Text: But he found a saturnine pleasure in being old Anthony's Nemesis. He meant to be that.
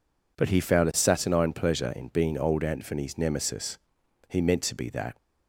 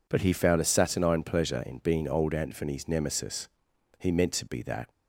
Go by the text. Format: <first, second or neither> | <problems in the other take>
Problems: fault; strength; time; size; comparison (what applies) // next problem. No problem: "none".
neither | none